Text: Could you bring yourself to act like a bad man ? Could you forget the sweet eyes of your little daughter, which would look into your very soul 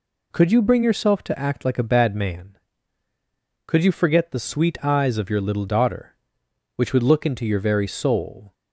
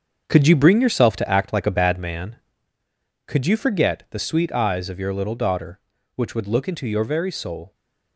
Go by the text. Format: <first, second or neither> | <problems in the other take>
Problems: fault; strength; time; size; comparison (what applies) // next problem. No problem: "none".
first | gets quieter; strong; throughout; 8.5 dB